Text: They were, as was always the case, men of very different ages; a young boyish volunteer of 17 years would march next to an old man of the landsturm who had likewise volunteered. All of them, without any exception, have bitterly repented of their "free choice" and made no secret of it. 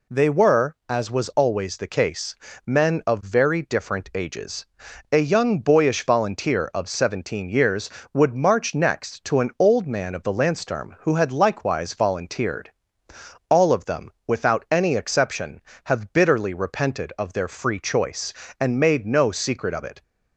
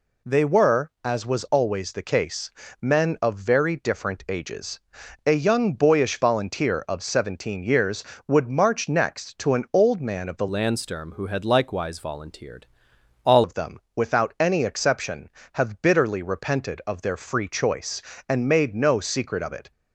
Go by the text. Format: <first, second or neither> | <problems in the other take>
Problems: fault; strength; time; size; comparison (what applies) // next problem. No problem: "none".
first | changes voice from "landsturm" to "All"; from 10.4 to 13.4 s; 3.0 s long